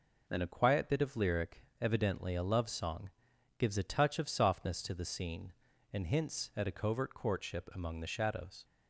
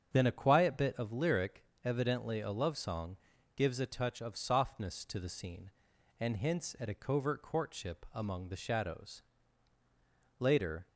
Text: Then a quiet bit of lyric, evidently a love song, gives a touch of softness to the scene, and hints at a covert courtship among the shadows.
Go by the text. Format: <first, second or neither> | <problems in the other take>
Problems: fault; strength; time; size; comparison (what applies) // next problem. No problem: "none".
first | starts louder than the rest; strong; until 1.1 s; 8 dB // goes on to say "Later"; slight; from 10.3 s on; 0.48 s long